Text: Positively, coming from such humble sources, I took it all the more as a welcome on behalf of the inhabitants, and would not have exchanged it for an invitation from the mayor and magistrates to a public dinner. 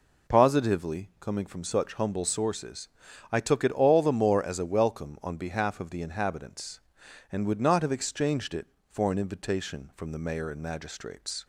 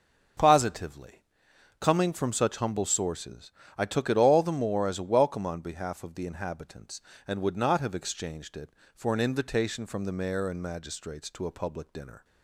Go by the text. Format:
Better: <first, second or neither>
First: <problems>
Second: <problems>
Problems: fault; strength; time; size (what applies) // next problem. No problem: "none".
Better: second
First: stops before "to a public dinner"; at 11.4 s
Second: none